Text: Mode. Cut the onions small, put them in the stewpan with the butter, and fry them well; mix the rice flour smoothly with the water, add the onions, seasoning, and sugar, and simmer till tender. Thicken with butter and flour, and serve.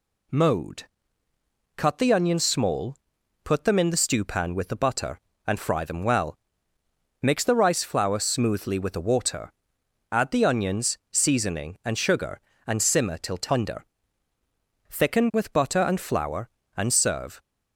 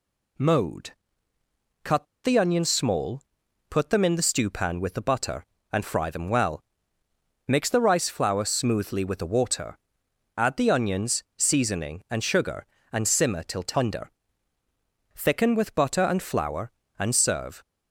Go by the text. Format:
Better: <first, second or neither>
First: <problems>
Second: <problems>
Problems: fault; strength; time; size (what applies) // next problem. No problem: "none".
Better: first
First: none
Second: pauses between "Cut" and "the"; slight; at 2.0 s; 0.18 s long